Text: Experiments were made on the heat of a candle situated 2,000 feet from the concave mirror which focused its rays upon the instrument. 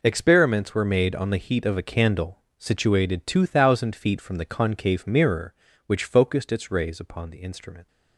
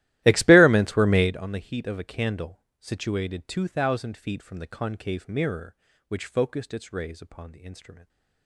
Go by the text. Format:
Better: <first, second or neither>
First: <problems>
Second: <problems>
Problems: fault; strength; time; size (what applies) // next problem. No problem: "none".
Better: first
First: pauses between "candle" and "situated"; slight; at 2.3 s; 0.20 s long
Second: starts louder than the rest; strong; until 1.3 s; 15 dB // pauses between "candle" and "situated"; slight; at 2.6 s; 0.20 s long